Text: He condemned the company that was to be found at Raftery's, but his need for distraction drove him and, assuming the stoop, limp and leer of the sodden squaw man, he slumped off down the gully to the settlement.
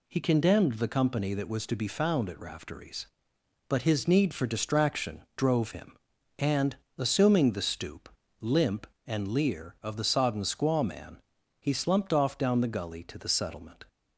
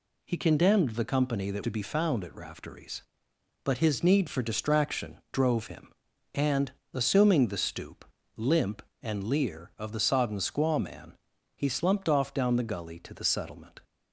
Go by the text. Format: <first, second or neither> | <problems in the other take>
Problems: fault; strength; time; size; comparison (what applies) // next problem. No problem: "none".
first | skips "was"; at 1.6 s